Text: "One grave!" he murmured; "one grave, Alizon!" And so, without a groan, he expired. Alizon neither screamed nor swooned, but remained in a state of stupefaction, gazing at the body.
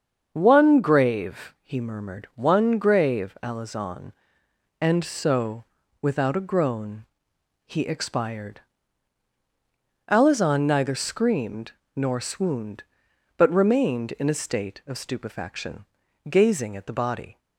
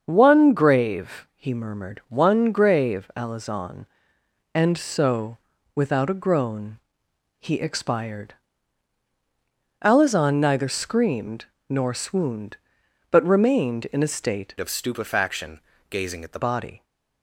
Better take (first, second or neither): first